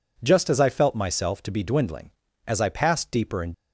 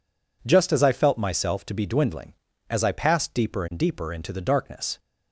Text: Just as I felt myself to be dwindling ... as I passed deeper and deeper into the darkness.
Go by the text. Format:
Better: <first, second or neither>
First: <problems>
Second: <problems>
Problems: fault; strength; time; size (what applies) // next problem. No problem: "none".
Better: second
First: stops before "deeper into the darkness"; at 3.5 s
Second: none